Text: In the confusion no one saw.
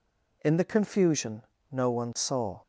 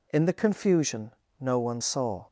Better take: neither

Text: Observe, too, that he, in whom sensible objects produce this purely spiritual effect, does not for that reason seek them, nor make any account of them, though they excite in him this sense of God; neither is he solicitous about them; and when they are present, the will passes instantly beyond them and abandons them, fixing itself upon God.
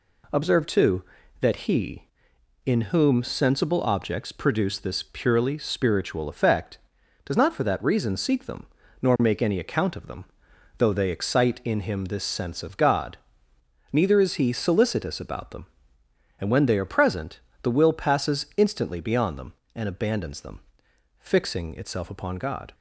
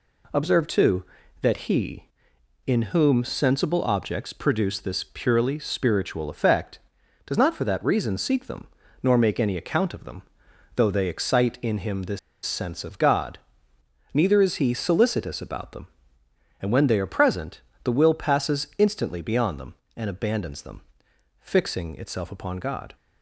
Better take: first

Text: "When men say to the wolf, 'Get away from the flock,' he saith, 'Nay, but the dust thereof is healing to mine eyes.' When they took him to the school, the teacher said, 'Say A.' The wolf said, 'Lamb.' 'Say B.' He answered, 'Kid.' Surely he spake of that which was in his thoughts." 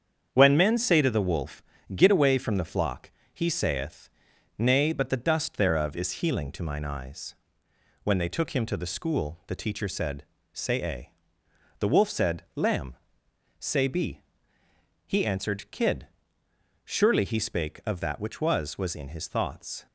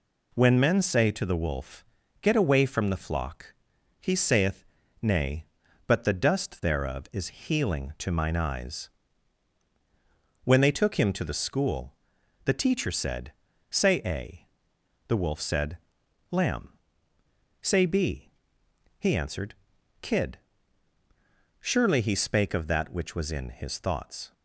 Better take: second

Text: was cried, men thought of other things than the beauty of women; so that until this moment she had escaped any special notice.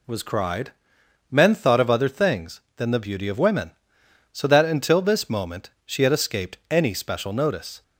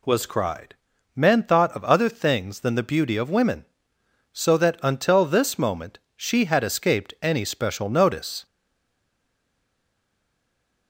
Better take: first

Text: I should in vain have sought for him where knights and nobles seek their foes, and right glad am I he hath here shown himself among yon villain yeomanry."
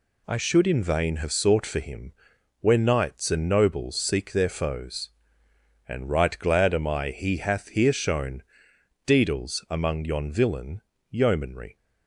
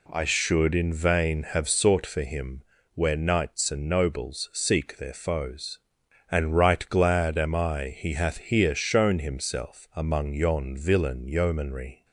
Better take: second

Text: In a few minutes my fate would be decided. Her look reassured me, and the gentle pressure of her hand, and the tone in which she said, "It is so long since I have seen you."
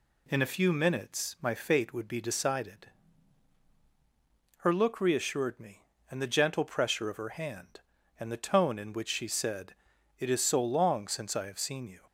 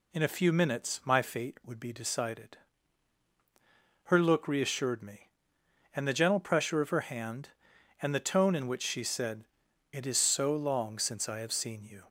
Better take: neither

